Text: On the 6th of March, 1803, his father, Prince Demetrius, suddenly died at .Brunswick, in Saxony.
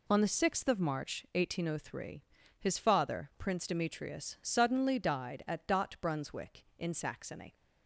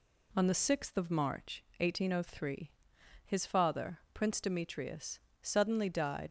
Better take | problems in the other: first | stops before "at Brunswick in Saxony"; at 6.2 s

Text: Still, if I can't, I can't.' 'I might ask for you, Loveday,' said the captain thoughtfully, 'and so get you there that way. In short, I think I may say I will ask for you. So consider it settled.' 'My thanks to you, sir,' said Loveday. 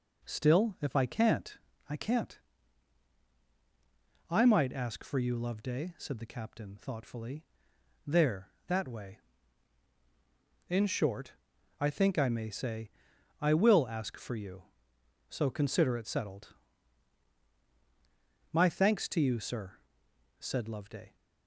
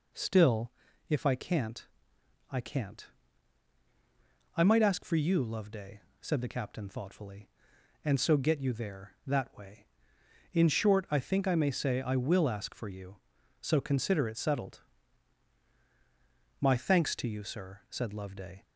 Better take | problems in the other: second | skips "and so get you"; at 7.7 s // pauses between "say" and "I"; noticeable; at 12.8 s; 0.52 s long

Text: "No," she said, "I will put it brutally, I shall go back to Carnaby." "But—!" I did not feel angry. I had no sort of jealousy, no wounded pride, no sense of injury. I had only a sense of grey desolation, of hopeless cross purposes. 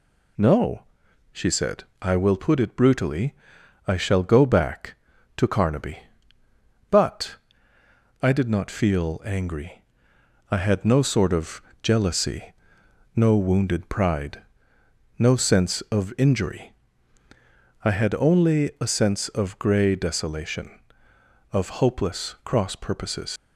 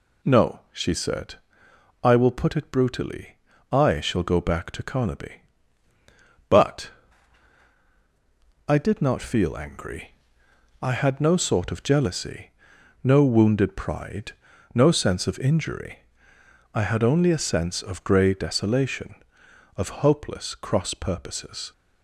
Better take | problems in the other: second | pauses between "of" and "jealousy"; slight; at 11.6 s; 0.22 s long // leaves "purposes" unfinished; at 23.3 s; 90 ms

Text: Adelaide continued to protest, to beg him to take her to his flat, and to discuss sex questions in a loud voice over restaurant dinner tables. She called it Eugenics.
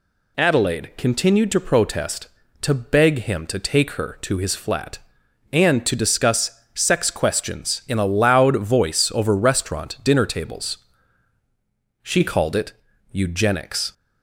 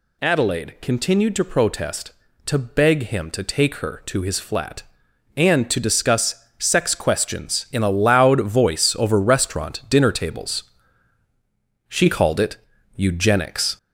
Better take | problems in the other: first | gets louder; noticeable; throughout; 4 dB // pauses between "it" and "Eugenics"; at 12.5 s; 0.40 s long; also in the first

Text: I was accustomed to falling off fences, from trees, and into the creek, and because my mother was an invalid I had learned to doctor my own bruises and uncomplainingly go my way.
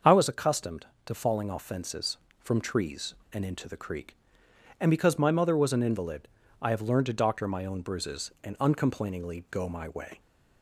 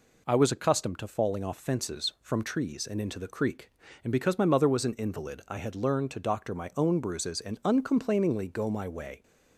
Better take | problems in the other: second | starts louder than the rest; until 1.2 s; 6.5 dB // pauses between "invalid" and "I"; slight; at 6.2 s; 0.34 s long // says "have" for "had"; at 6.6 s

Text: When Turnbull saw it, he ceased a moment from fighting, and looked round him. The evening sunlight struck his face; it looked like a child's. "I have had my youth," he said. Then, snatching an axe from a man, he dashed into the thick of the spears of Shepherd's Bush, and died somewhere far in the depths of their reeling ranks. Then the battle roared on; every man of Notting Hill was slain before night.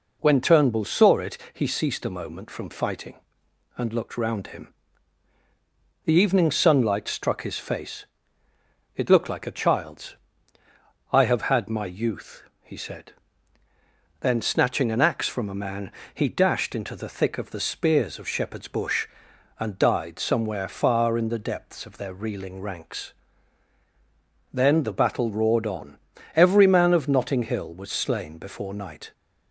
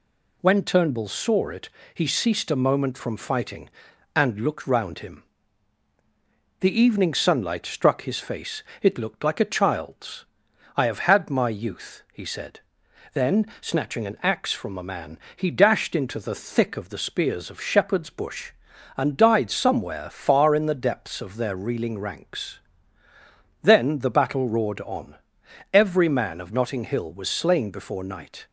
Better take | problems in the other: neither | none

